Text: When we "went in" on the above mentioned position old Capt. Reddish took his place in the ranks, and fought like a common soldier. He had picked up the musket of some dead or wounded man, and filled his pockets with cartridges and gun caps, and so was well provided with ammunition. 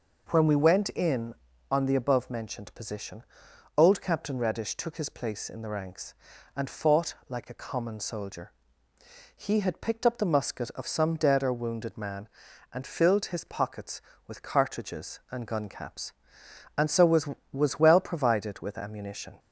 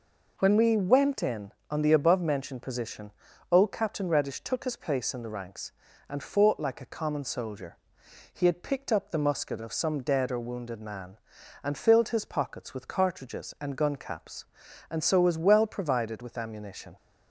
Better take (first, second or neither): second